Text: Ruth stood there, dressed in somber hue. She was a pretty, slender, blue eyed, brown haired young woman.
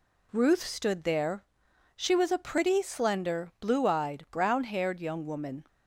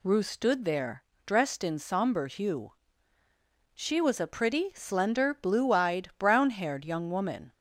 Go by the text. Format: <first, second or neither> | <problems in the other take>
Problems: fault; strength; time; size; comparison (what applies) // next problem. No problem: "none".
second | skips "dressed in somber hue"; at 1.6 s